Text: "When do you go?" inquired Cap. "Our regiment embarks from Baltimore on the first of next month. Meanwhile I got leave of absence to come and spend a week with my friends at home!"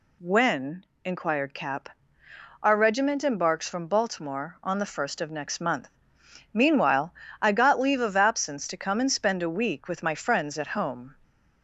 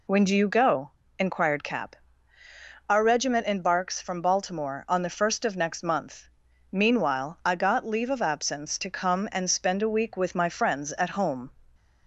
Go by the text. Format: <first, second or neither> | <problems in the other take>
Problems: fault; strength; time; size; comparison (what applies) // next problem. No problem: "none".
second | skips "do you go"; at 0.9 s // pauses between "Meanwhile" and "I"; slight; at 7.1 s; 0.28 s long